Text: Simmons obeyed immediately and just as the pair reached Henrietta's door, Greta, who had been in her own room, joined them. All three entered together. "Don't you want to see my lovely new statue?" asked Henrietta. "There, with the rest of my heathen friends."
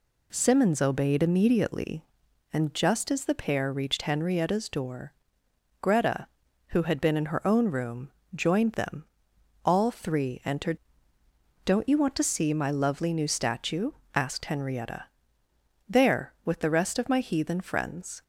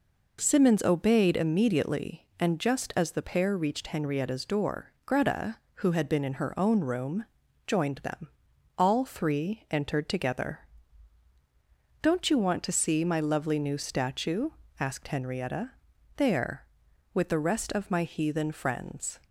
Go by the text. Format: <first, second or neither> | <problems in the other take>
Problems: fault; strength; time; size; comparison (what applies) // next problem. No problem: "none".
second | skips "together"; at 11.2 s